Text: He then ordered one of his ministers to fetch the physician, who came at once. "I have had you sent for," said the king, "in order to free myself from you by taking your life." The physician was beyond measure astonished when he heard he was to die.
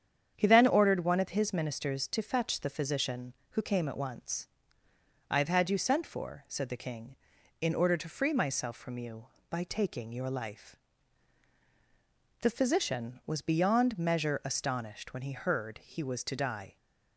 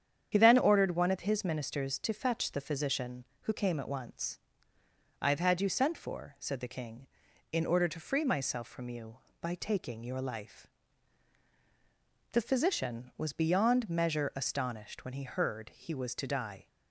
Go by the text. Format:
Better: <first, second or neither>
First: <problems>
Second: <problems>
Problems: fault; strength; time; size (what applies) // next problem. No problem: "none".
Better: first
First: starts louder than the rest; strong; until 1.3 s; 8.5 dB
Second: loses the start of "He"; at 0.3 s; 45 ms // starts louder than the rest; strong; until 1.3 s; 8.5 dB